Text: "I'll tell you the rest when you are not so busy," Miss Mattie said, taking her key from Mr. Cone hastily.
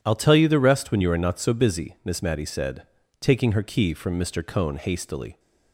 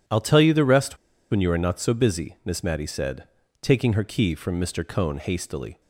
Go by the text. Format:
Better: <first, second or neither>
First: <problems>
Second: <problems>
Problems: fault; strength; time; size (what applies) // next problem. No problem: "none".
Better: first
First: none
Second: pauses between "rest" and "when"; slight; at 0.9 s; 0.34 s long